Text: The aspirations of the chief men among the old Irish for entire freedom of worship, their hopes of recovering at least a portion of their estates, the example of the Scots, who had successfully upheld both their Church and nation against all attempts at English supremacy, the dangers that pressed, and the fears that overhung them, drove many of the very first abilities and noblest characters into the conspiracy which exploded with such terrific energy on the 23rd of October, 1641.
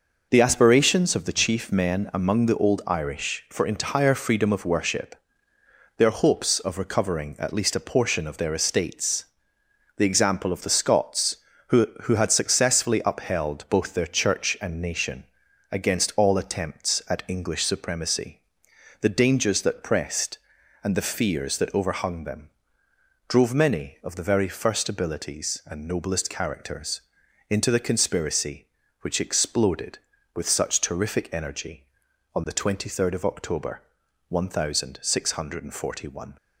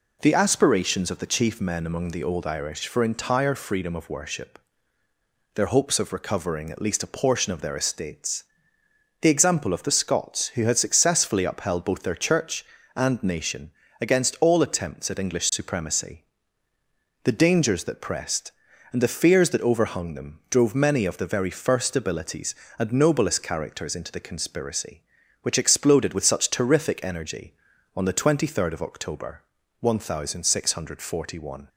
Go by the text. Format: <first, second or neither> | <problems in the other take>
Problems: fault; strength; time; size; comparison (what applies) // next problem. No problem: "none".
second | says "who" twice; at 12.0 s // pauses between "nation" and "against"; noticeable; at 15.2 s; 0.46 s long; slight in the second // pauses between "characters" and "into"; noticeable; at 27.0 s; 0.50 s long